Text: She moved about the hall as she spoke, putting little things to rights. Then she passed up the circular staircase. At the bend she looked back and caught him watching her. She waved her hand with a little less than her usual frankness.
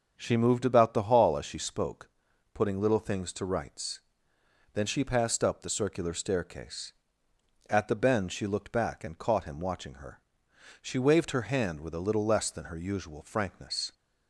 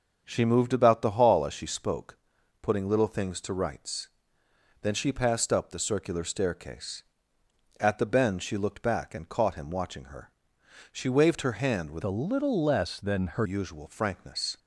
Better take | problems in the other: first | starts louder than the rest; until 1.2 s; 6.5 dB; also in the first // changes voice from "a" to "her"; from 12.0 to 13.4 s; 1.4 s long

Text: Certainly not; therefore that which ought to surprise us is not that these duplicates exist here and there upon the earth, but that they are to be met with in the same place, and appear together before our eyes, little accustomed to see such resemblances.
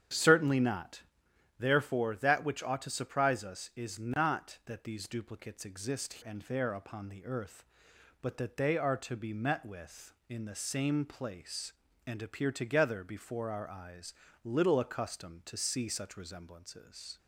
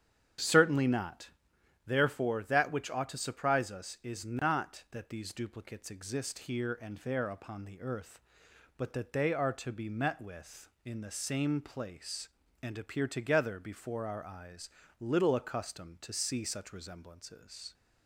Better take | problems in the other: second | starts louder than the rest; strong; until 1.6 s; 9 dB; strong in the second // skips "here"; at 6.2 s

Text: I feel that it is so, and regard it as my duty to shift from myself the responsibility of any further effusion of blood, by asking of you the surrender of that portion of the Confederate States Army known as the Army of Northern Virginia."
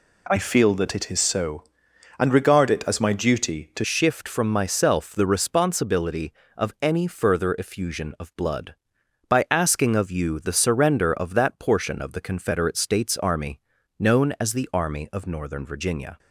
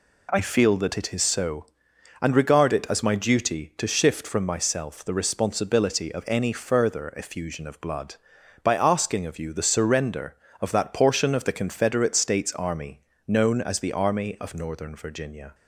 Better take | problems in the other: second | changes voice at "shift"; from 3.8 s on; 12.3 s long // pauses between "Army" and "known"; slight; at 13.6 s; 0.36 s long; slight in the second

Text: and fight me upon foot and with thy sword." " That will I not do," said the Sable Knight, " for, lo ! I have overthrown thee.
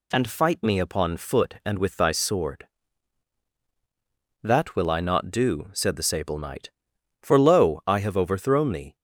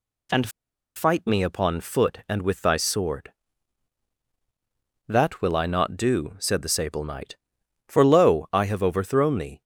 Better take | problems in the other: first | pauses between "and" and "fight"; noticeable; at 0.4 s; 0.47 s long

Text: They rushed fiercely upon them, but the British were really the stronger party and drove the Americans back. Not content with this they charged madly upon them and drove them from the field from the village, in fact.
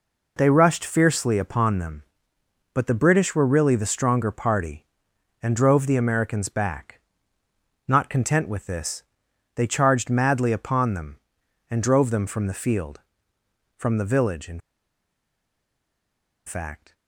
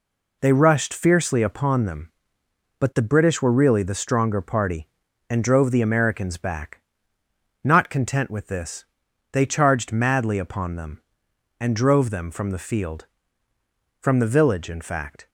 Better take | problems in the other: second | pauses between "this" and "they"; noticeable; at 9.0 s; 0.52 s long; noticeable in the second // pauses between "in" and "fact"; strong; at 14.5 s; 1.8 s long

